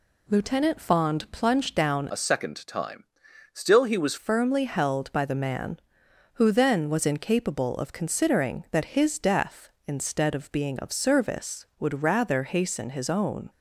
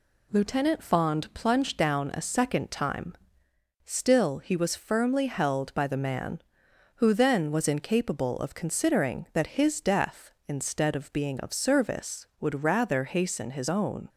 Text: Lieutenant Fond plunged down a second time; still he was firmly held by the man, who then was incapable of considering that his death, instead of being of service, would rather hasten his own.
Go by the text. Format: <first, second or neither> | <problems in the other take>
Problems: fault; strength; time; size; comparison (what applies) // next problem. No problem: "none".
second | changes voice from "a" to "was"; from 2.1 to 4.1 s; 2.0 s long